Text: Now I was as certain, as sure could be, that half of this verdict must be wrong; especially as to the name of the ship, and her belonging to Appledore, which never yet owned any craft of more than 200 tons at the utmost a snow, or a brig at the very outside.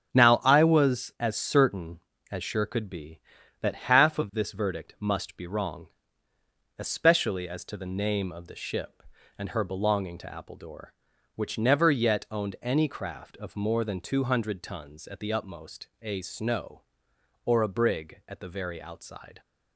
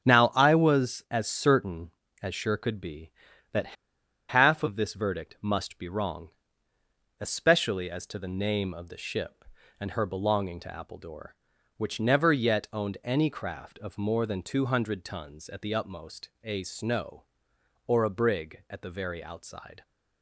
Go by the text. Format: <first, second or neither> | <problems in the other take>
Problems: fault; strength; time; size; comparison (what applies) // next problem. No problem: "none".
first | starts louder than the rest; strong; until 1.1 s; 8 dB; strong in the first // pauses between "that" and "half"; noticeable; at 3.7 s; 0.56 s long